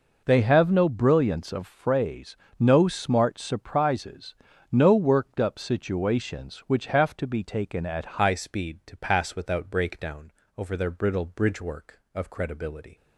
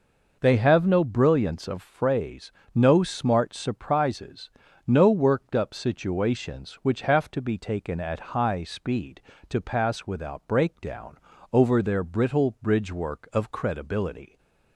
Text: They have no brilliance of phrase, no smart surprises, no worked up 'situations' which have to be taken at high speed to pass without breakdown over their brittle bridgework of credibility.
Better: second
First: changes voice at "high"; from 8.2 s on; 4.7 s long // pauses between "breakdown" and "over"; slight; at 10.3 s; 0.26 s long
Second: pauses between "breakdown" and "over"; slight; at 11.1 s; 0.34 s long

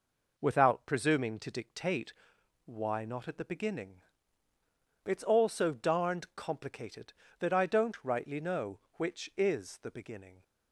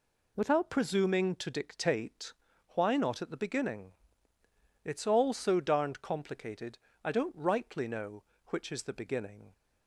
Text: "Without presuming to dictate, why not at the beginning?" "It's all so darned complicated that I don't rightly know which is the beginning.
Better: first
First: none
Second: skips "that"; at 6.9 s

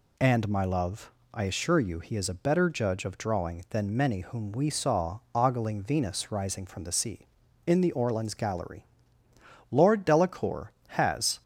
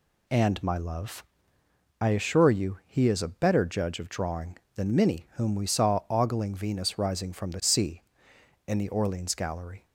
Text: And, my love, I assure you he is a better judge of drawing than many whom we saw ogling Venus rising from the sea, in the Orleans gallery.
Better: second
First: pauses between "saw" and "ogling"; slight; at 5.1 s; 0.16 s long // goes on to say "Lord Delacour has"; strong; from 9.7 s on; 1.7 s long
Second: none

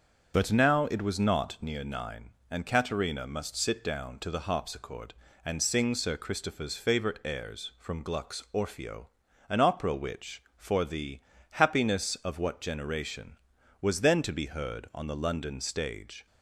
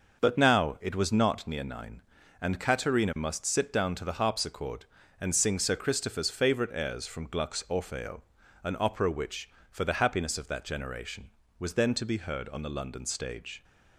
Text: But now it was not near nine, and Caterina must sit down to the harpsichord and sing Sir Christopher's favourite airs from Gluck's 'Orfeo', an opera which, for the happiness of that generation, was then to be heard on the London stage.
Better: second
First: starts louder than the rest; strong; until 1.3 s; 7 dB // pauses between "the" and "happiness"; slight; at 11.1 s; 0.32 s long // says "what" for "that"; at 12.3 s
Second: none

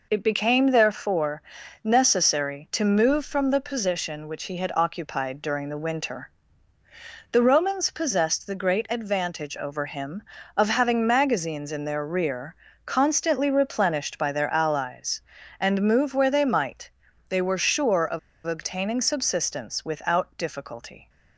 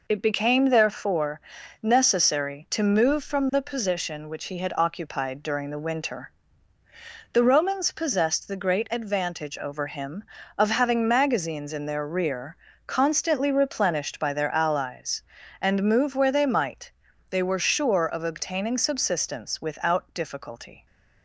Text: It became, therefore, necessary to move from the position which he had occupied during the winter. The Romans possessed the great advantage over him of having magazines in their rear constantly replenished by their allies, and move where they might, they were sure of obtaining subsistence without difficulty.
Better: second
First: pauses between "rear" and "constantly"; slight; at 12.5 s; 0.30 s long // pauses between "of" and "obtaining"; slight; at 18.1 s; 0.27 s long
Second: pauses between "rear" and "constantly"; slight; at 12.5 s; 0.30 s long

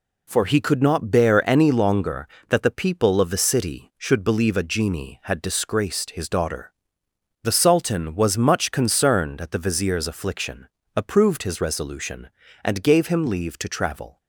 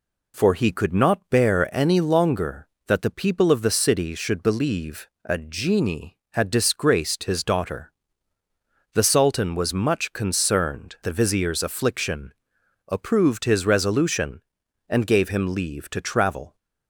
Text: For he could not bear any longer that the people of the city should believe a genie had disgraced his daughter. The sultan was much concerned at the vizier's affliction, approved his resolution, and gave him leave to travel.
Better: first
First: none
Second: pauses between "believe" and "a"; slight; at 5.0 s; 0.16 s long // skips "at"; at 10.9 s

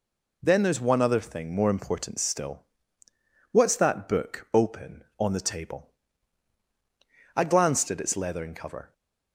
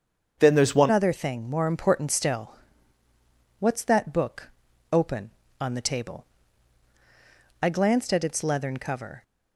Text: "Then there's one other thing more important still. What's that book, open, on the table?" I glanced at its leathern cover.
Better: first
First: none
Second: starts louder than the rest; until 1.4 s; 6.5 dB // changes voice at "other"; from 0.9 s on; 8.3 s long

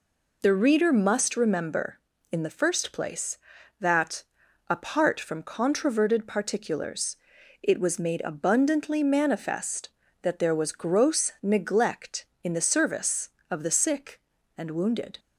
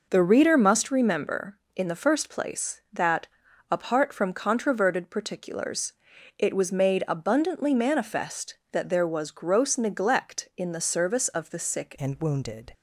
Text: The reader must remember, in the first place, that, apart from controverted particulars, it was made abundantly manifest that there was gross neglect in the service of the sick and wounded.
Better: first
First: none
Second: changes voice at "and"; from 11.9 s on; 0.8 s long

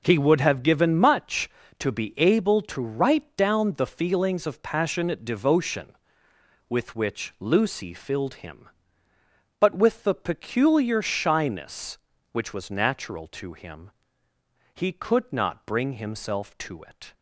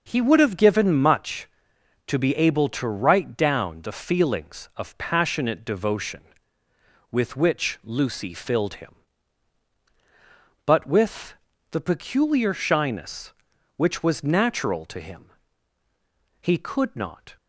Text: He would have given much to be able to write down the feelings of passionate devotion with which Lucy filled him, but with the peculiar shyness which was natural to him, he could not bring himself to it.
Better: first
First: none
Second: pauses between "with" and "the"; slight; at 11.3 s; 0.36 s long // stops before "bring himself to it"; at 17.3 s

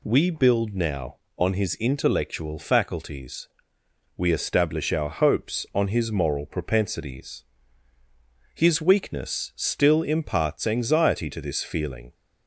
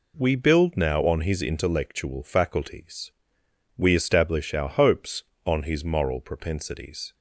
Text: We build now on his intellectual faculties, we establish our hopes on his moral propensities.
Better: second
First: goes on to say "His weakness still imparts anxiety to this feeling"; strong; from 8.5 s on; 3.5 s long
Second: none

